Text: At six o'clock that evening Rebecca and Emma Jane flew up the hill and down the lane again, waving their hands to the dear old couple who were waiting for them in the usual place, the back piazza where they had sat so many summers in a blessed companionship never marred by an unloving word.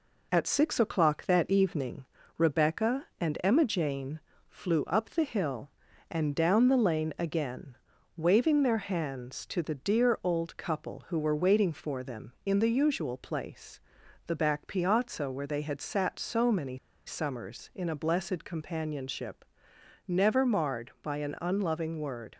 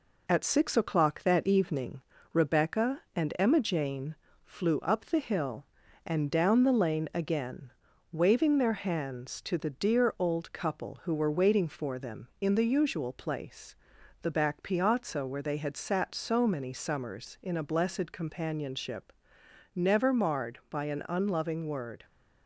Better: second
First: pauses between "evening" and "Rebecca"; slight; at 2.0 s; 0.32 s long // pauses between "Jane" and "flew"; slight; at 4.1 s; 0.28 s long // pauses between "many" and "summers"; slight; at 16.7 s; 0.28 s long // pauses between "companionship" and "never"; noticeable; at 19.4 s; 0.62 s long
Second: pauses between "evening" and "Rebecca"; slight; at 2.0 s; 0.31 s long // pauses between "Jane" and "flew"; slight; at 4.1 s; 0.28 s long // pauses between "companionship" and "never"; noticeable; at 19.1 s; 0.62 s long

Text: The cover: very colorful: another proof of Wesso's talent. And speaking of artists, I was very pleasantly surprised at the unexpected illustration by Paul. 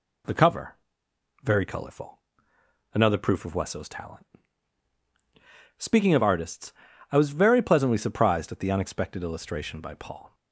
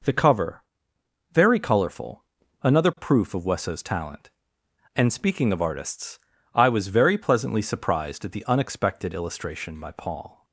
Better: second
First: skips "And"; at 5.0 s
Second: none

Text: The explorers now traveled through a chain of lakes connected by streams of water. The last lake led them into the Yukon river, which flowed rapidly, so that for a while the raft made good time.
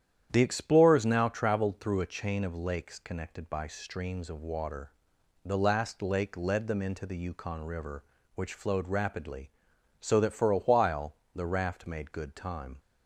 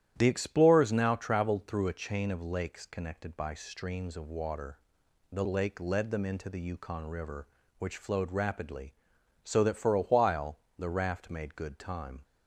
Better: first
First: starts louder than the rest; strong; until 1.3 s; 9.5 dB // pauses between "while" and "the"; slight; at 11.1 s; 0.18 s long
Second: starts louder than the rest; strong; until 1.1 s; 11.5 dB // skips "last"; at 5.4 s // pauses between "while" and "the"; slight; at 10.5 s; 0.18 s long

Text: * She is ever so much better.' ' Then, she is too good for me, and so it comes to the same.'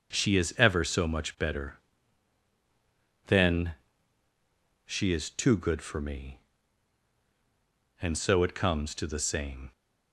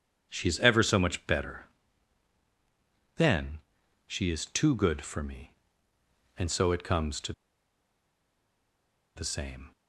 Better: first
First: starts louder than the rest; until 1.1 s; 6 dB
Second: starts louder than the rest; strong; until 1.3 s; 7 dB // pauses between "to" and "the"; strong; at 7.3 s; 1.8 s long

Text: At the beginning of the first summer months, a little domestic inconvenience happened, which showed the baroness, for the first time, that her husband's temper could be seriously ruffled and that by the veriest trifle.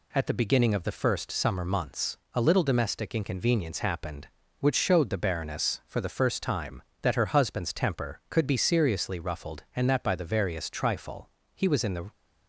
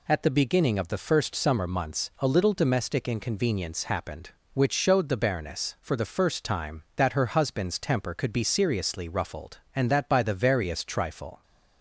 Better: second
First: goes on to say "He was in the"; from 11.5 s on; 0.56 s long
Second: none

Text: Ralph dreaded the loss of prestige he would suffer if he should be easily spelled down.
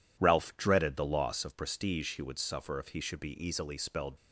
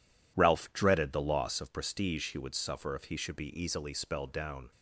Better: second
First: stops before "down"; at 4.1 s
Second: none

